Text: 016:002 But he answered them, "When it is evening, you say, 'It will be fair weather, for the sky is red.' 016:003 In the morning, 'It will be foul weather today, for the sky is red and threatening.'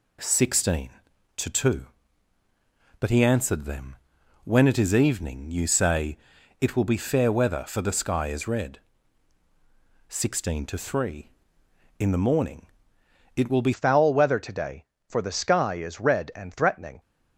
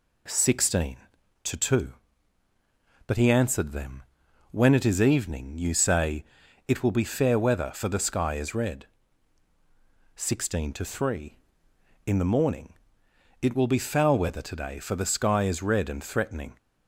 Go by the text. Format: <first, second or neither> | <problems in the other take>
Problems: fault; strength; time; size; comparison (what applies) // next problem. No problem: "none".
second | changes voice at "foul"; from 13.7 s on; 3.2 s long